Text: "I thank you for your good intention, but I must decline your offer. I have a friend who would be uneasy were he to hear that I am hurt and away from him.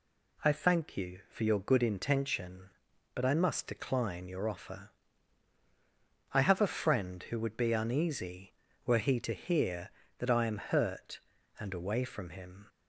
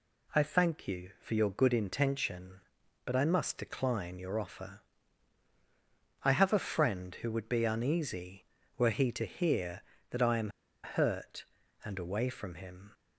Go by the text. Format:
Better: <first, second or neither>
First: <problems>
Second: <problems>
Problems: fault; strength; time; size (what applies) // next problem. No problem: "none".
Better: first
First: none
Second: pauses between "am" and "hurt"; slight; at 10.4 s; 0.34 s long